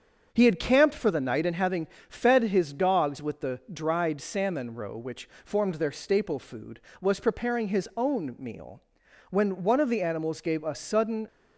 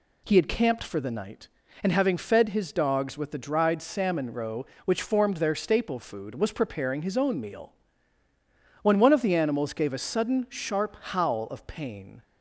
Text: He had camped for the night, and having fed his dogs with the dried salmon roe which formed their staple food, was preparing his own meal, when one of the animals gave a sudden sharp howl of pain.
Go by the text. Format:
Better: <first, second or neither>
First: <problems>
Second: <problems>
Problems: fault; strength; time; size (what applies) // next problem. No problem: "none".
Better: second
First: starts louder than the rest; strong; until 1.3 s; 7 dB // pauses between "having" and "fed"; slight; at 1.8 s; 0.22 s long // stops before "sharp howl of pain"; at 11.2 s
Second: none